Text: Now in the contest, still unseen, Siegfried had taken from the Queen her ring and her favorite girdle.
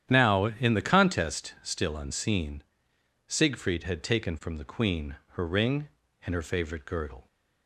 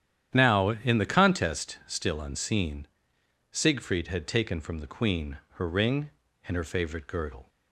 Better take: neither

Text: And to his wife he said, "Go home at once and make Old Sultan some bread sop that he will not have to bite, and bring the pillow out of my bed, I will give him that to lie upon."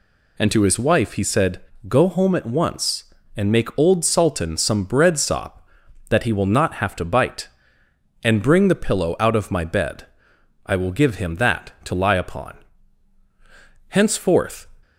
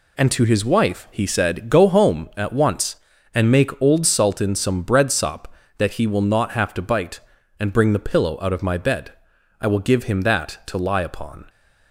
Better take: second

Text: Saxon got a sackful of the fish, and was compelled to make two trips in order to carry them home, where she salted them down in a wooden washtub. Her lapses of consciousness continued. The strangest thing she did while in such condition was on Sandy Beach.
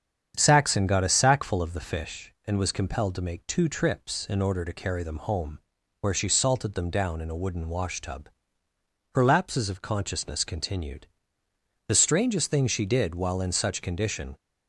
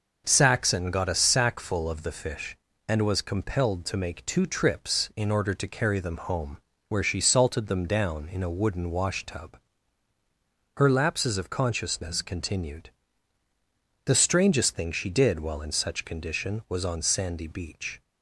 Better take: second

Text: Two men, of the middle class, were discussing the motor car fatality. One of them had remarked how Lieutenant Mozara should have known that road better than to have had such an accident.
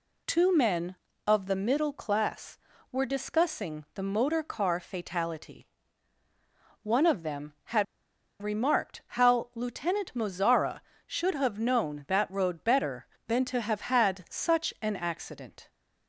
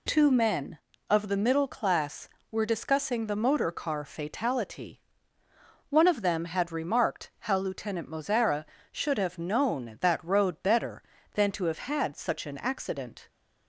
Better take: second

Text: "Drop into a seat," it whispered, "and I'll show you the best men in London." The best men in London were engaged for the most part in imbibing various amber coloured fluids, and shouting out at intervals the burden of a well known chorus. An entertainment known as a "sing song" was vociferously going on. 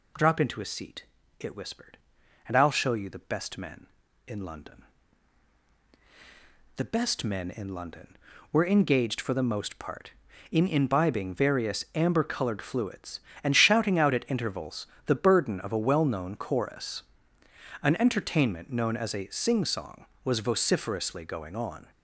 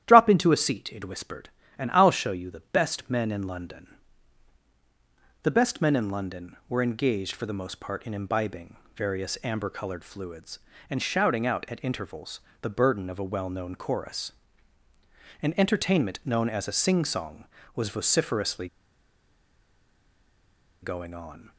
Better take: first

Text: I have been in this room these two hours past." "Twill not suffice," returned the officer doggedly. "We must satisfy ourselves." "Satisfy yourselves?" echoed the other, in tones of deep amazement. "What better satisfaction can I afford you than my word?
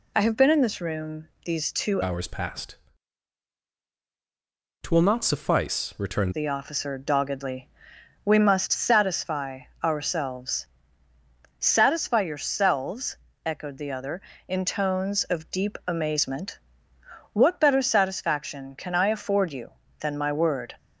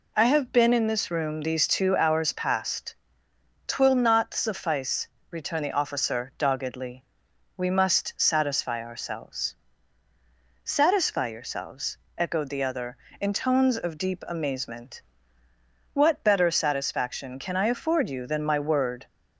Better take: second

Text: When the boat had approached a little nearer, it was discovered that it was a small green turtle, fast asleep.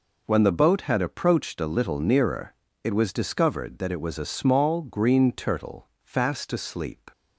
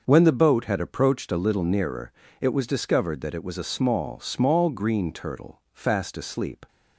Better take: first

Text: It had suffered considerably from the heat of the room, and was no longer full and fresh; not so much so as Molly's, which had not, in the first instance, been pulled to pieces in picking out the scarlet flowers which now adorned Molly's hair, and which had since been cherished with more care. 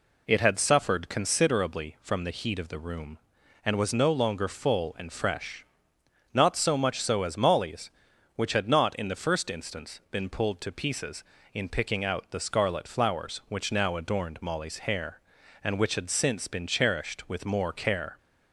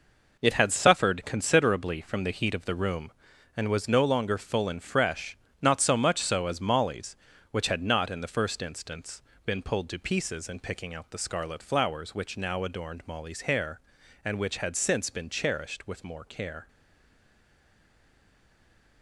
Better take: first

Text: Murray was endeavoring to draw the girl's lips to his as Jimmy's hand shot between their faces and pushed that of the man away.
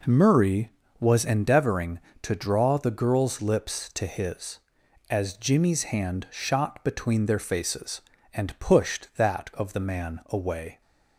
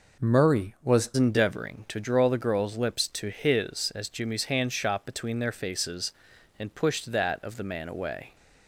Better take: first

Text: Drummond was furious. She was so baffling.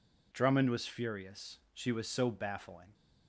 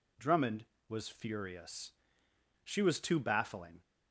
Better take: first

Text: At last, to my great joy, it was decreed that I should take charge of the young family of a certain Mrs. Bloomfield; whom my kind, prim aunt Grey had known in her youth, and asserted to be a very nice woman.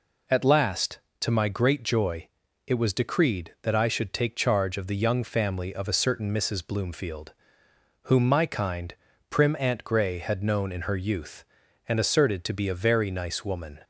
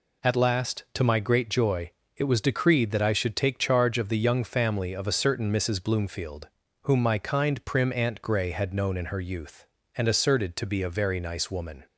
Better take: neither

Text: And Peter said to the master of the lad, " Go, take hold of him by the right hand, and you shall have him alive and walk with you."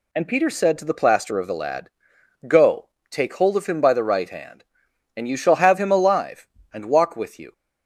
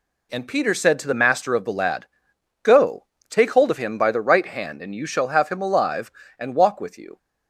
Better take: second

